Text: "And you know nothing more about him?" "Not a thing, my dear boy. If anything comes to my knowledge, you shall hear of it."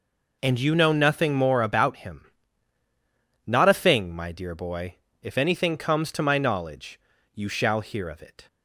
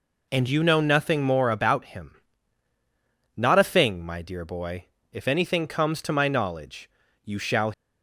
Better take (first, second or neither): first